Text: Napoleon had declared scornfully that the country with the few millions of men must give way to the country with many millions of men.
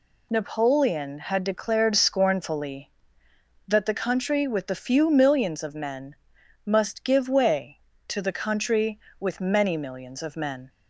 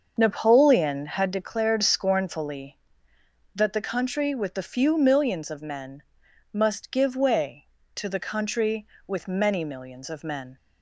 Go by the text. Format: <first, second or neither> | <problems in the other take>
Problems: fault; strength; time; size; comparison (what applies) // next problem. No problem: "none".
first | starts louder than the rest; until 1.4 s; 6 dB // pauses between "men" and "must"; noticeable; at 6.0 s; 0.52 s long; noticeable in the first